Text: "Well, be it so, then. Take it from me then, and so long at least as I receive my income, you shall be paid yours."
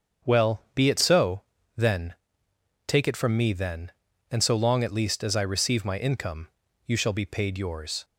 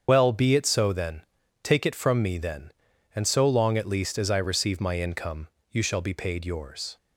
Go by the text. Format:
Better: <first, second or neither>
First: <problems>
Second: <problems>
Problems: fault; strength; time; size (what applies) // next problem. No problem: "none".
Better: first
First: starts louder than the rest; strong; until 1.3 s; 7 dB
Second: loses the start of "Well"; at 0.0 s; 60 ms // starts louder than the rest; strong; until 1.0 s; 7.5 dB